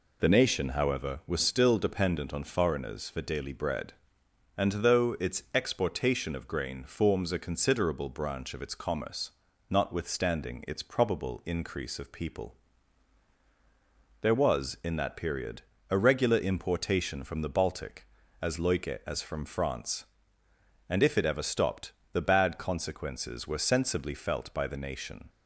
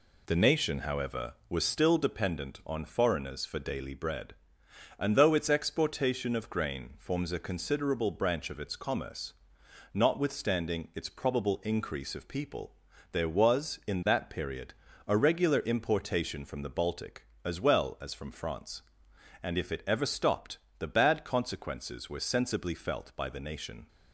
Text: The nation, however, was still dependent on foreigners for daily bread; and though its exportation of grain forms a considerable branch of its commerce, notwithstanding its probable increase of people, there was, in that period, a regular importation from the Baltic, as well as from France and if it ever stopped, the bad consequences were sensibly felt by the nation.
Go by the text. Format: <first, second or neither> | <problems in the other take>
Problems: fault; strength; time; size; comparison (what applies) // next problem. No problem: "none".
second | says "loike" for "well"; at 18.5 s